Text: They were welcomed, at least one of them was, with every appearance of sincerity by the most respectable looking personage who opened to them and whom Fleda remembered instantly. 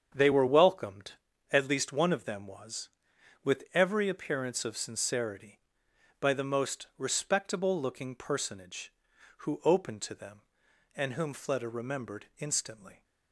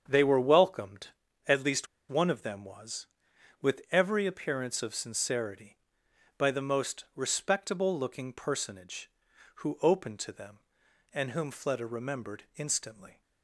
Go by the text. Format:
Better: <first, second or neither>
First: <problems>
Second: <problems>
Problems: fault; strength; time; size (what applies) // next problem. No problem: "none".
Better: first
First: starts louder than the rest; strong; until 1.5 s; 8.5 dB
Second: starts louder than the rest; strong; until 1.0 s; 8 dB // pauses between "least" and "one"; slight; at 1.8 s; 0.22 s long